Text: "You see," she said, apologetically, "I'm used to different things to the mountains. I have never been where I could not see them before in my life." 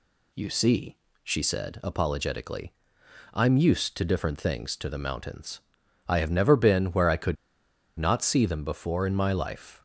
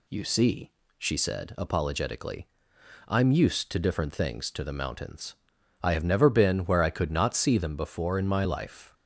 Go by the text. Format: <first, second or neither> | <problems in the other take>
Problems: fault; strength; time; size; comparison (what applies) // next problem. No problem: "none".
second | pauses between "could" and "not"; noticeable; at 7.3 s; 0.64 s long